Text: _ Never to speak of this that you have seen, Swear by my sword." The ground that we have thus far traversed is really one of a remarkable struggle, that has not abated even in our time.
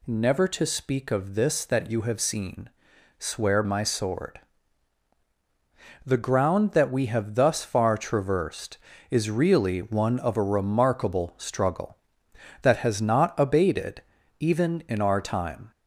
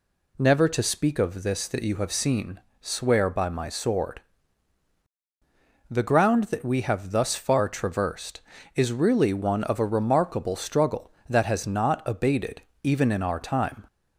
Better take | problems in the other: second | skips "by"; at 3.6 s // pauses between "abated" and "even"; at 14.0 s; 0.38 s long; slight in the second

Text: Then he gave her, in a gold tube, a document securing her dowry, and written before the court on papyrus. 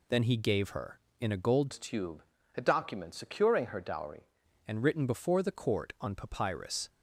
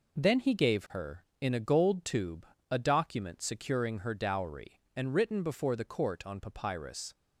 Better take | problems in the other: second | changes voice from "tube" to "dowry"; from 1.7 to 4.2 s; 2.5 s long

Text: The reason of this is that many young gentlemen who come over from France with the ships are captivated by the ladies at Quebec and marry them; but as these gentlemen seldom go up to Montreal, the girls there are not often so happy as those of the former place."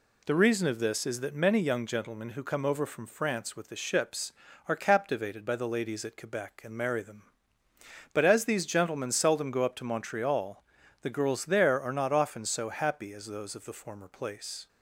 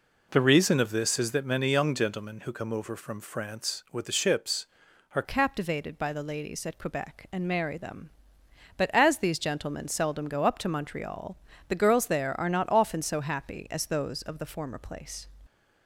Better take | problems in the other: first | changes voice at "captivated"; from 5.2 s on; 10.0 s long

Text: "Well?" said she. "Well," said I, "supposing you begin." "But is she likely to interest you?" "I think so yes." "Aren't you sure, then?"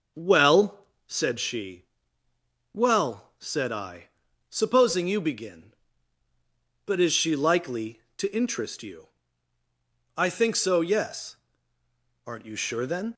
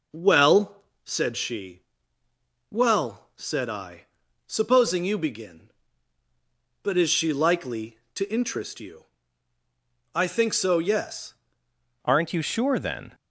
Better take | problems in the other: first | changes voice at "Aren't"; from 12.0 s on; 1.1 s long

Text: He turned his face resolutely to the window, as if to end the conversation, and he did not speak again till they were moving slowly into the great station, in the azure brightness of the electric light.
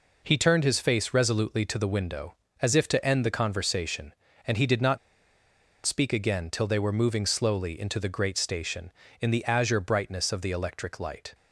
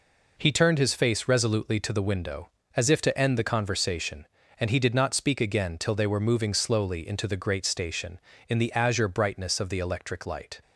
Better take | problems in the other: second | pauses between "not" and "speak"; noticeable; at 4.9 s; 0.87 s long

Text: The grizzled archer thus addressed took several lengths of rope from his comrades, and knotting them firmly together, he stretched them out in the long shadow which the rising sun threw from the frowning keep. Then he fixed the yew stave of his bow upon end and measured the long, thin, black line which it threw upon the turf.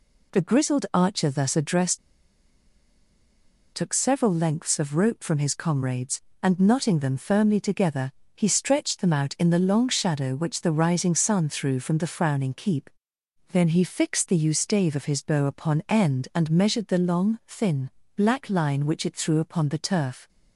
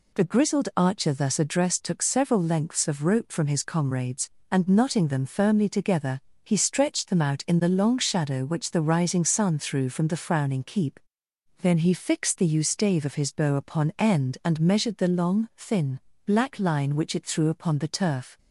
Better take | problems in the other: second | pauses between "addressed" and "took"; strong; at 1.9 s; 1.7 s long

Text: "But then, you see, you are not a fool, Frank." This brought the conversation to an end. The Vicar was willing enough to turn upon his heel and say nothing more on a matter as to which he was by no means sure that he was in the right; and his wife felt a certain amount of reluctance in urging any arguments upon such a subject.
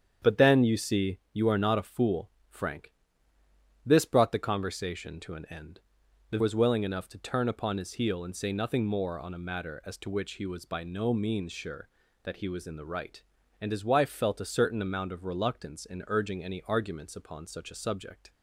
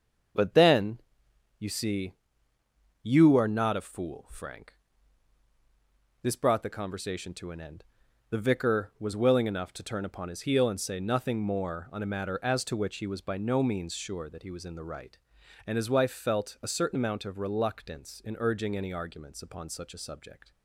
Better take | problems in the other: second | starts louder than the rest; strong; until 1.3 s; 8 dB; also in the second // skips "Vicar"; at 6.3 s

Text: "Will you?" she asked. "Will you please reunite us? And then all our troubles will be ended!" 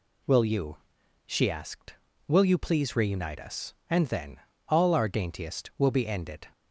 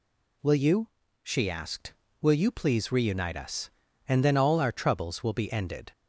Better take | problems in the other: second | pauses between "then" and "all"; slight; at 4.3 s; 0.30 s long // says "daintiest" for "troubles"; at 5.0 s

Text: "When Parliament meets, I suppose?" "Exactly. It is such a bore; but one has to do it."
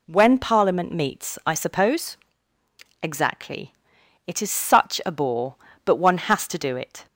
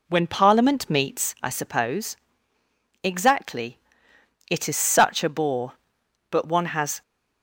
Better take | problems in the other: first | stops before "to do it"; at 7.0 s

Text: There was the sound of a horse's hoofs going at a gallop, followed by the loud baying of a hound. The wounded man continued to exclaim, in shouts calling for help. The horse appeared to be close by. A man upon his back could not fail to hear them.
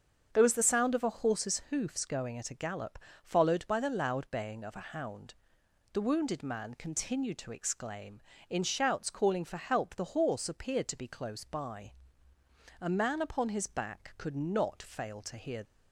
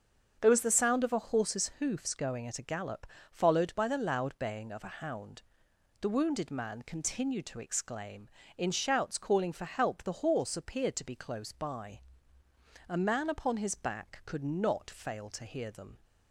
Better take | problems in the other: second | starts louder than the rest; strong; until 1.3 s; 7 dB; strong in the second // stops before "them"; at 15.6 s

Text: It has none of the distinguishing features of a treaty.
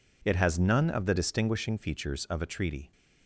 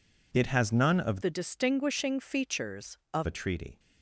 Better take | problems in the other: first | changes voice from "the" to "of"; from 1.2 to 3.2 s; 2.0 s long

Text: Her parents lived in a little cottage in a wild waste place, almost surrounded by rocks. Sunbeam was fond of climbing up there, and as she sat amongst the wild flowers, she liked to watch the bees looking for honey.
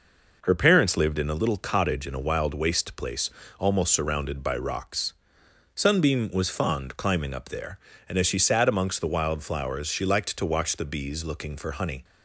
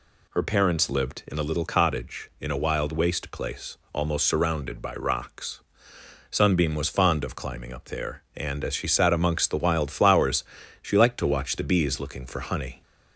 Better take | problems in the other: second | skips "of"; at 6.9 s

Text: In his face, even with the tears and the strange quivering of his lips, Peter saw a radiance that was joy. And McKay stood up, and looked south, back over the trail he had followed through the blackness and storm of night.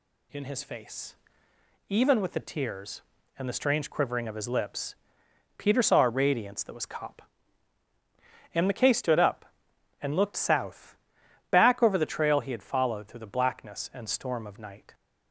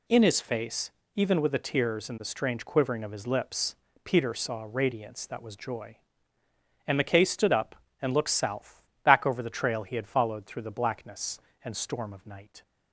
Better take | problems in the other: second | says "cop" for "joy"; at 6.8 s

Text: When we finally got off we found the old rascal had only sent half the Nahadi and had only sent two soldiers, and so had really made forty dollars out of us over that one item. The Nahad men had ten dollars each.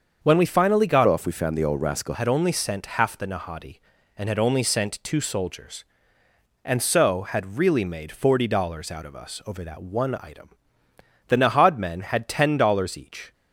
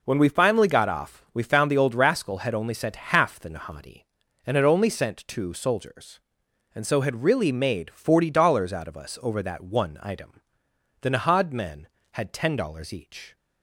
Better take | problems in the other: second | starts louder than the rest; until 1.2 s; 6.5 dB // changes voice from "off" to "rascal"; from 1.0 to 2.1 s; 1.1 s long

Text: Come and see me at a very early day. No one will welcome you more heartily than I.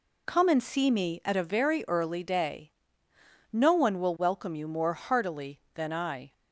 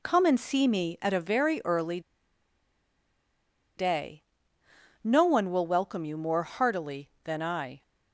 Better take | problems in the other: first | pauses between "early" and "day"; strong; at 1.9 s; 1.7 s long

